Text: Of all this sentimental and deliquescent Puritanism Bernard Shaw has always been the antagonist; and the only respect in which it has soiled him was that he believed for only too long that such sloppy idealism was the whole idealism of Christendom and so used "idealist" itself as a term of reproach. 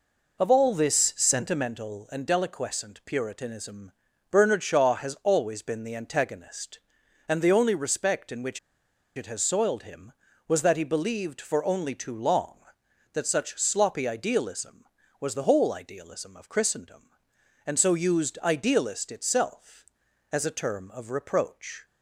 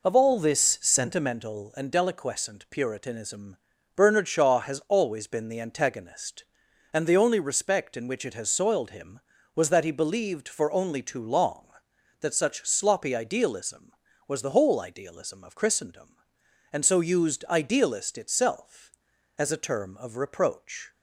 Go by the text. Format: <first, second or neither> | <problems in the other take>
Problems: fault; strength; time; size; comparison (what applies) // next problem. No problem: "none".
second | pauses between "Puritanism" and "Bernard"; at 3.9 s; 0.40 s long; also in the second // pauses between "which" and "it"; noticeable; at 8.5 s; 0.57 s long